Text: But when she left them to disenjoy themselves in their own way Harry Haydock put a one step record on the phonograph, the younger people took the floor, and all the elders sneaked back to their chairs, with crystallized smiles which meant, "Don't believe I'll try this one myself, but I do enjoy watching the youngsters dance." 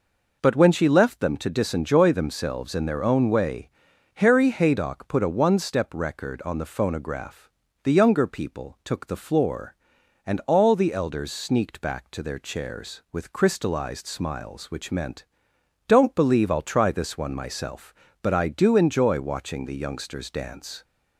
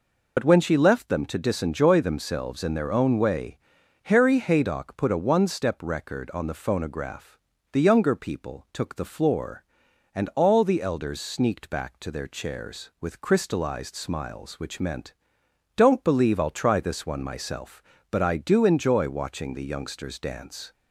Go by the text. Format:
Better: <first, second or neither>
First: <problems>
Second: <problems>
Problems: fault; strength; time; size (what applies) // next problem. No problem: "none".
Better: first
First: pauses between "way" and "Harry"; noticeable; at 3.6 s; 0.48 s long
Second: loses the start of "But"; at 0.3 s; 70 ms // pauses between "way" and "Harry"; noticeable; at 3.5 s; 0.48 s long